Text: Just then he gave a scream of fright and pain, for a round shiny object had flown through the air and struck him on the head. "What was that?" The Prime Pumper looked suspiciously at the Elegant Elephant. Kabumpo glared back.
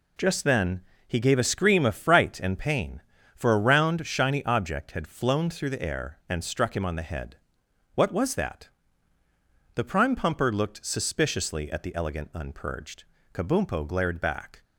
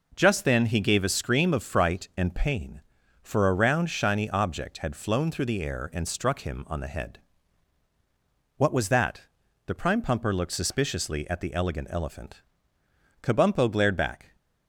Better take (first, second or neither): second